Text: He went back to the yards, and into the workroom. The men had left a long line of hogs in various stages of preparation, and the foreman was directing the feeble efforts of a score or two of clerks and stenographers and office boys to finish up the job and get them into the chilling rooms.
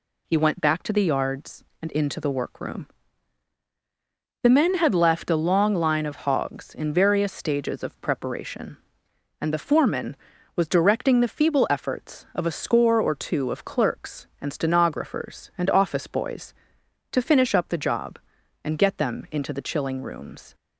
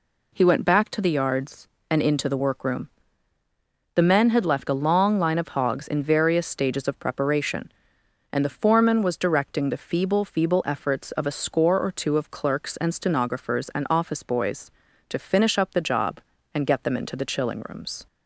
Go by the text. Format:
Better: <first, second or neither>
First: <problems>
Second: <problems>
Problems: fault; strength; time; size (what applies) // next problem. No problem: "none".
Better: first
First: none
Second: says "feeble" twice; at 10.2 s